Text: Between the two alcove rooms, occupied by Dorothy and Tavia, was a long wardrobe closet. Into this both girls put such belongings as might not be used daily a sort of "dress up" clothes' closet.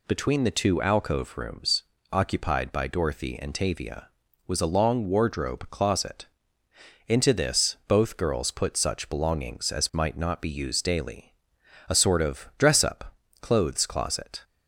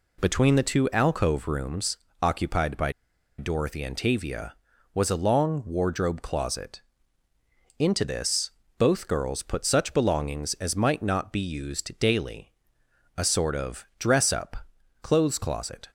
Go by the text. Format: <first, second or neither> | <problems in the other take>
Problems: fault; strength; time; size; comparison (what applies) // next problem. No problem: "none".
first | pauses between "by" and "Dorothy"; noticeable; at 2.9 s; 0.47 s long // pauses between "this" and "both"; slight; at 8.4 s; 0.28 s long // pauses between "daily" and "a"; noticeable; at 12.5 s; 0.64 s long; noticeable in the first // pauses between "up" and "clothes"; noticeable; at 14.5 s; 0.48 s long; slight in the first